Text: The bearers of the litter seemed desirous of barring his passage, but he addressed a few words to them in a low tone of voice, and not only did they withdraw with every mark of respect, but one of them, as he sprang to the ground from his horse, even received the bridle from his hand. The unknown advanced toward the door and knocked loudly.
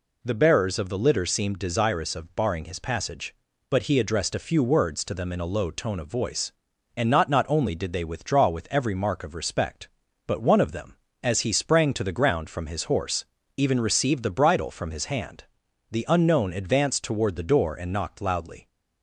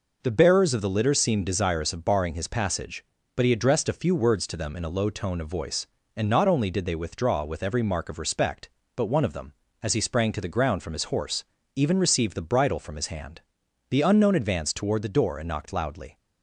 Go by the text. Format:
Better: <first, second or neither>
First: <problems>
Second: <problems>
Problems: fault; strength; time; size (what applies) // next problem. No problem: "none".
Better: second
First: says "not" twice; at 7.2 s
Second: none